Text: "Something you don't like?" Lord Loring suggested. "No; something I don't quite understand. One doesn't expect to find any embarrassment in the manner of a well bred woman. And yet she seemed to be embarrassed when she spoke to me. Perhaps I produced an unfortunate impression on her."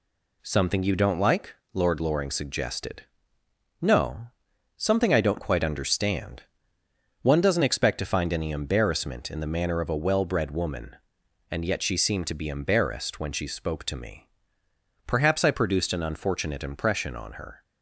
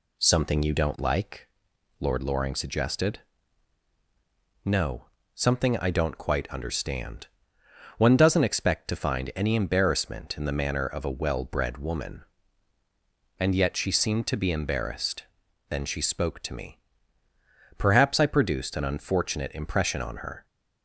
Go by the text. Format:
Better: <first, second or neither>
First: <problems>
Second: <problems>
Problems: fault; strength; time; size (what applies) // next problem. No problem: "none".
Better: first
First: none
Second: says "then" for "when"; at 15.6 s